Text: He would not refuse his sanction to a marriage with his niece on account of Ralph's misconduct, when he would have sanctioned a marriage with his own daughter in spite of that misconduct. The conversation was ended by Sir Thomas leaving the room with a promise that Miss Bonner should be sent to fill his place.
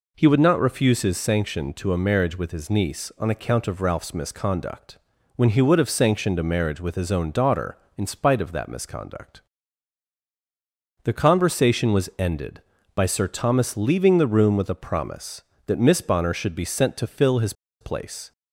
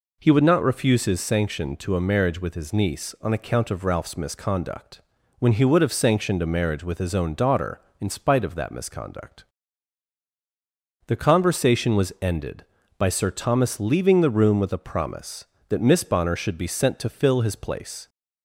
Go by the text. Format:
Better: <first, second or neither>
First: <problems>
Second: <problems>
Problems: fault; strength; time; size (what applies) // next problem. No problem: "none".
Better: second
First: pauses between "his" and "place"; slight; at 17.5 s; 0.28 s long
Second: none